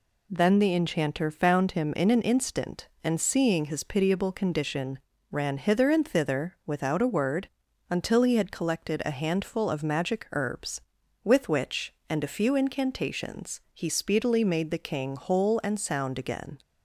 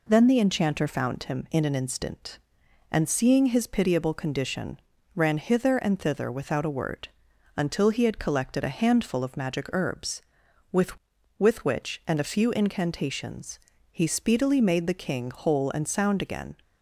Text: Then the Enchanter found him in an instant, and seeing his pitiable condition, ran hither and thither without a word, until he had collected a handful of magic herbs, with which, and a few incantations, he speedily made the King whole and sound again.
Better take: first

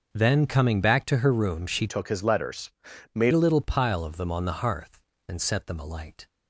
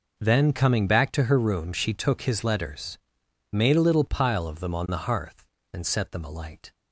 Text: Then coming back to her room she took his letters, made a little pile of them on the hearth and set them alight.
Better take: second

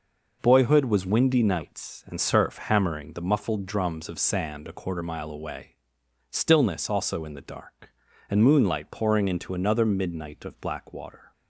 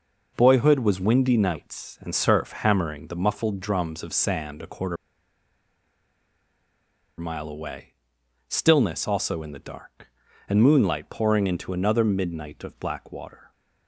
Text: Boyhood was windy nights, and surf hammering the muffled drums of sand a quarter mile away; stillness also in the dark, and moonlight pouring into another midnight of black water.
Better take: first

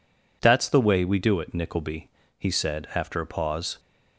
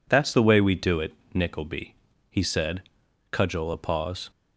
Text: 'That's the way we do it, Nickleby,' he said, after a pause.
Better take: first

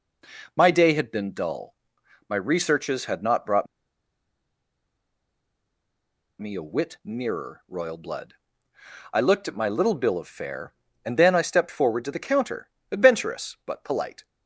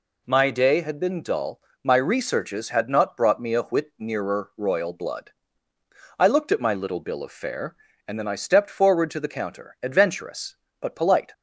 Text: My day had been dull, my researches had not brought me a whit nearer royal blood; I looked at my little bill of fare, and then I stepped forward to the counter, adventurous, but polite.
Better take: second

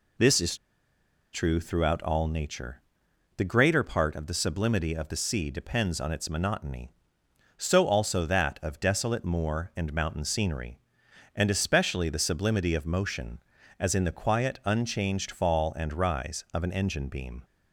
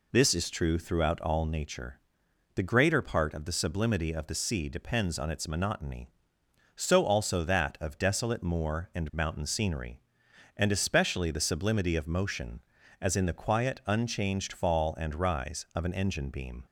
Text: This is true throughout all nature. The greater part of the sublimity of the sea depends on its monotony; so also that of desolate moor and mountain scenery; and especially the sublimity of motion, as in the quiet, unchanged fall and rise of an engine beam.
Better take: second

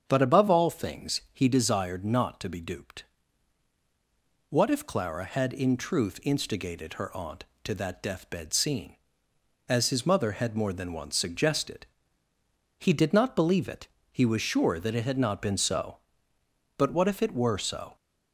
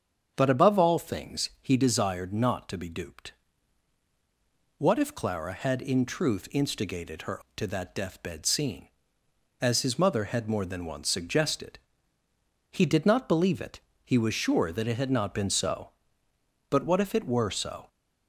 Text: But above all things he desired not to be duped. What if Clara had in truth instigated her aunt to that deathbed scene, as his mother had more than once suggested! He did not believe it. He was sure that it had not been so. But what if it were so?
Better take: first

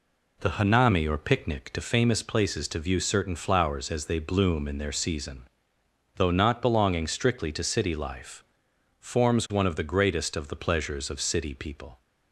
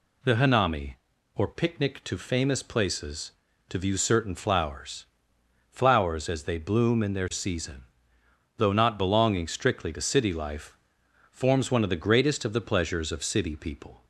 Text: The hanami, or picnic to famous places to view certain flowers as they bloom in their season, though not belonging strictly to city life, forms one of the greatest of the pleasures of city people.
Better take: first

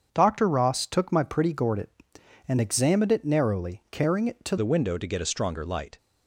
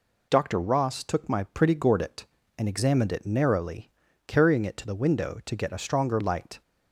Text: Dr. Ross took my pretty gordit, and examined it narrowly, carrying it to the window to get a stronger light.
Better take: second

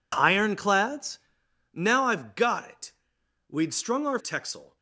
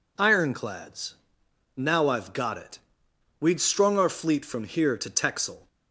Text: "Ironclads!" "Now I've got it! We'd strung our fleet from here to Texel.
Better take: second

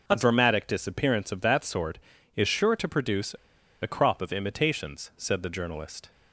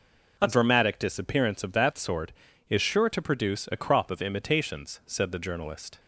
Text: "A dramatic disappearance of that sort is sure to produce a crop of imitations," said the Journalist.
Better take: second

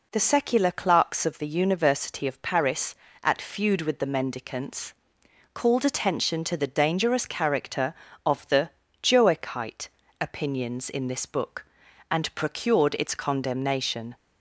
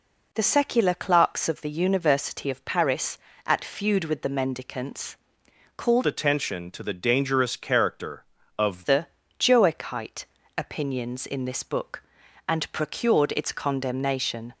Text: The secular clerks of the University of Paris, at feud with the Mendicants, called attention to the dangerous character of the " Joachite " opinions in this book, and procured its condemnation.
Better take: first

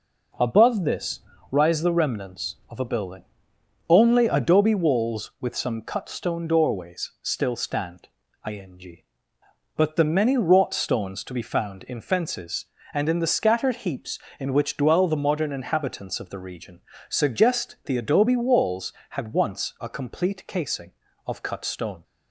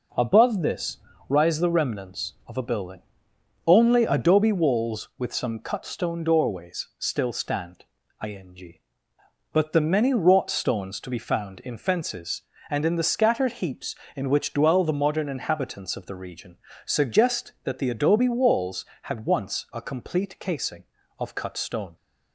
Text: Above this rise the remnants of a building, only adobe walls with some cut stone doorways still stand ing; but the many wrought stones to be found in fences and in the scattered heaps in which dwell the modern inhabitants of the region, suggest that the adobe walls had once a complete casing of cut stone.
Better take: second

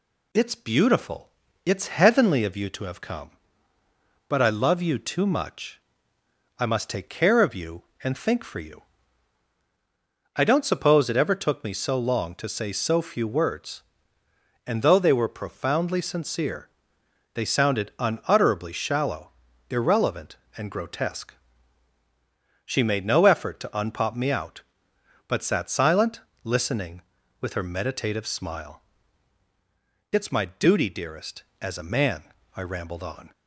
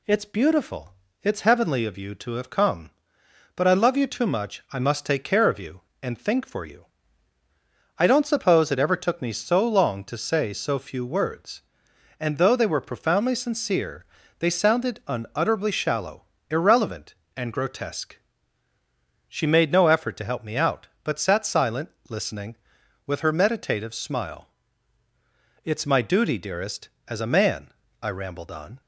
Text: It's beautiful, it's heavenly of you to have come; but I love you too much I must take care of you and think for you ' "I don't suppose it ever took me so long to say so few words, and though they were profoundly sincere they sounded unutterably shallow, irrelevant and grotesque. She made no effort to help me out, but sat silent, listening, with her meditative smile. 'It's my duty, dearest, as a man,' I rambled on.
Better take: second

